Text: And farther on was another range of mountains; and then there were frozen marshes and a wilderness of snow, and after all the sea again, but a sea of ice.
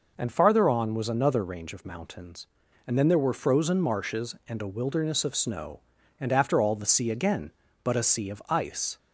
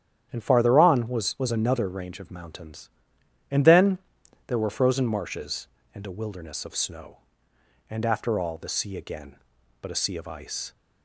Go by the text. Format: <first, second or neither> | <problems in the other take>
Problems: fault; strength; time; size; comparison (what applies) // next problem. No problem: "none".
first | starts louder than the rest; strong; until 1.3 s; 10 dB // says "was" twice; at 1.3 s // pauses between "then" and "there"; noticeable; at 3.9 s; 0.50 s long